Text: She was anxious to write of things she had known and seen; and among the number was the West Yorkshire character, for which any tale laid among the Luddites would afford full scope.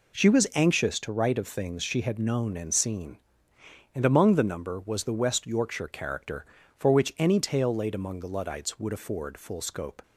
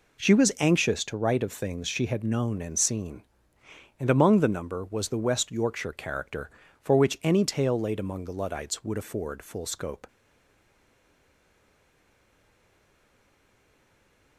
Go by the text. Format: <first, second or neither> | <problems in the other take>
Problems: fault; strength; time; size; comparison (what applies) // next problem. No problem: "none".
first | stays silent after the last word; strong; from 10.0 s on; 4.3 s long